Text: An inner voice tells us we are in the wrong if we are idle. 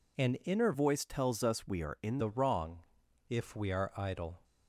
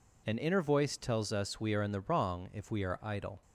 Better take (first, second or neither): second